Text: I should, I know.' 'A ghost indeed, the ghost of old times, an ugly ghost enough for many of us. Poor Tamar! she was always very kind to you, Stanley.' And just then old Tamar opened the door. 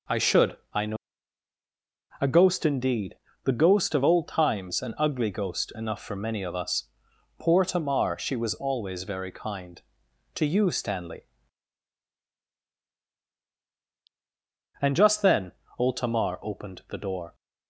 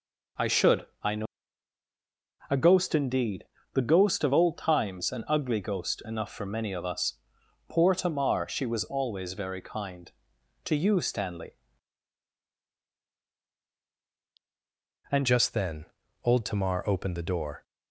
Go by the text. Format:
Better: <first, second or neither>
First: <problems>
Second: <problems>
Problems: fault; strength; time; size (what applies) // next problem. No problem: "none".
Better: first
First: pauses between "then" and "old"; slight; at 15.5 s; 0.26 s long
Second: changes voice at "just"; from 15.2 s on; 2.4 s long // pauses between "then" and "old"; at 15.8 s; 0.40 s long